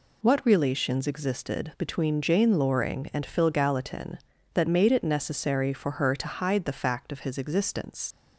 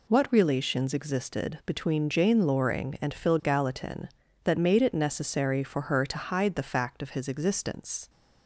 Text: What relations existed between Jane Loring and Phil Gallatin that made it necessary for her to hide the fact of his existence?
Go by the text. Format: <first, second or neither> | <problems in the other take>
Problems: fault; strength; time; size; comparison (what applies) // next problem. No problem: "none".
second | leaves "existence" unfinished; at 8.1 s; 85 ms